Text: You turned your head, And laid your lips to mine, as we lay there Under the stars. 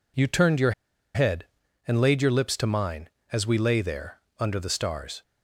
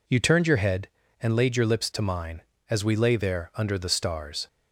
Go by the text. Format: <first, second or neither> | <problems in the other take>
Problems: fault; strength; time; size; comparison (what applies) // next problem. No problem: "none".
second | pauses between "your" and "head"; at 0.7 s; 0.43 s long // pauses between "there" and "Under"; slight; at 4.1 s; 0.20 s long